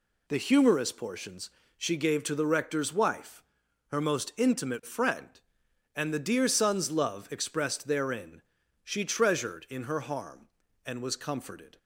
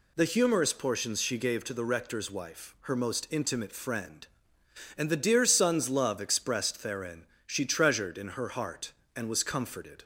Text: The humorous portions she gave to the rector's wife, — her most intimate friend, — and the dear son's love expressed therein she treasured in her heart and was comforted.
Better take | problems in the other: second | pauses between "portions" and "she"; slight; at 1.5 s; 0.26 s long // pauses between "therein" and "she"; at 8.4 s; 0.42 s long; slight in the second // says "harm" for "heart"; at 10.0 s

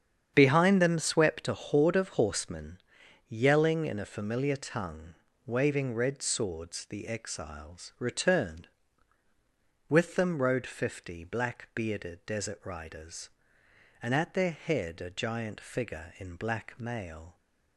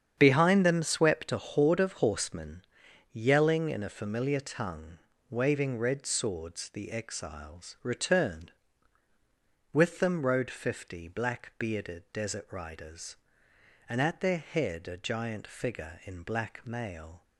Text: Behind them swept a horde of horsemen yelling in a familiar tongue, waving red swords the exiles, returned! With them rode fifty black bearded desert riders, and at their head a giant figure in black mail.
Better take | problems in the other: neither | starts louder than the rest; strong; the same in both // pauses between "horsemen" and "yelling"; noticeable; the same in both

